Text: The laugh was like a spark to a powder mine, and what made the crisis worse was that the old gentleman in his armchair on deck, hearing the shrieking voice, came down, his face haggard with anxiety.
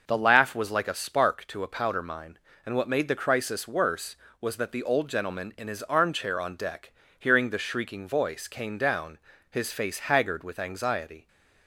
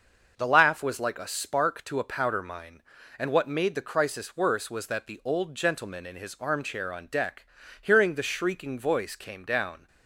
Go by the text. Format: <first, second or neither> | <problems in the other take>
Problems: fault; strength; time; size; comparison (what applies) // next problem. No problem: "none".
first | starts louder than the rest; until 1.3 s; 6 dB // stops before "his face haggard with anxiety"; at 9.8 s